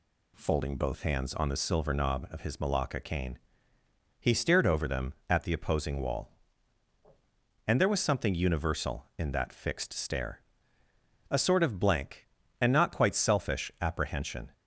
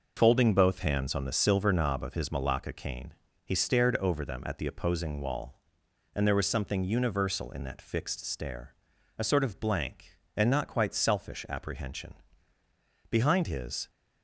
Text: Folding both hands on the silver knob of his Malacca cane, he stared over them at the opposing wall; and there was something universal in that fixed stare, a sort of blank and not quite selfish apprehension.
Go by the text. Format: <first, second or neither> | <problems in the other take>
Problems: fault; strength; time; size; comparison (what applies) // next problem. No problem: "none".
first | goes on to say "Behind his"; noticeable; from 13.1 s on; 0.78 s long